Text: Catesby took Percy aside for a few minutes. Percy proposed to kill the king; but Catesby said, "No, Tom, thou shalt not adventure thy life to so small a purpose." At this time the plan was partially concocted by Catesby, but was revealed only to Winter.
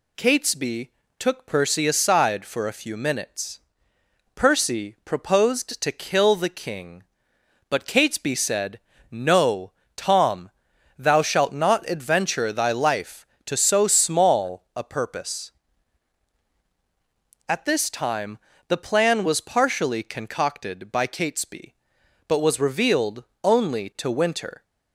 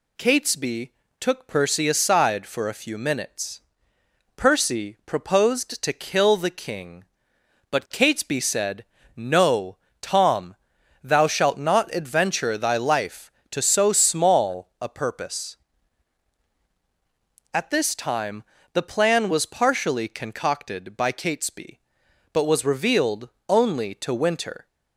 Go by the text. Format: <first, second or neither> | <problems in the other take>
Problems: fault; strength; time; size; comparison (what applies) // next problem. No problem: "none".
neither | pauses between "Catesby" and "took"; slight; the same in both // pauses between "time" and "the"; slight; the same in both // pauses between "revealed" and "only"; slight; the same in both